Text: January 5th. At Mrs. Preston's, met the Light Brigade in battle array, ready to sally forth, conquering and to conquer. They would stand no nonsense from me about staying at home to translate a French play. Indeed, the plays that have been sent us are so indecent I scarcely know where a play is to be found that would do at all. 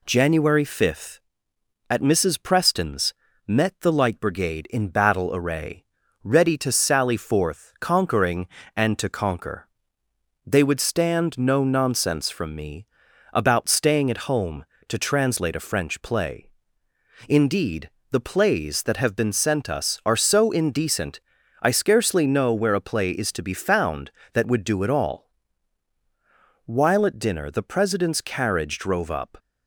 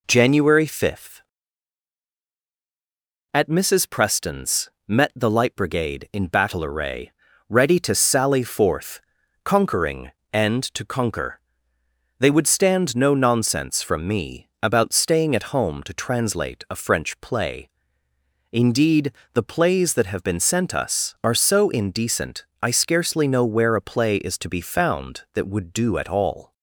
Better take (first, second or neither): second